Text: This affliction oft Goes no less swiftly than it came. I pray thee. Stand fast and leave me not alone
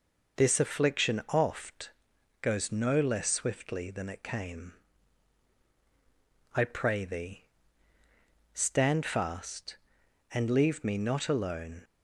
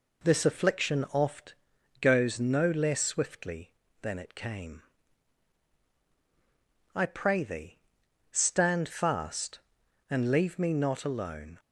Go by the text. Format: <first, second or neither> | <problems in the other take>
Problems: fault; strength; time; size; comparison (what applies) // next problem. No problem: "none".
neither | pauses between "oft" and "Goes"; noticeable; the same in both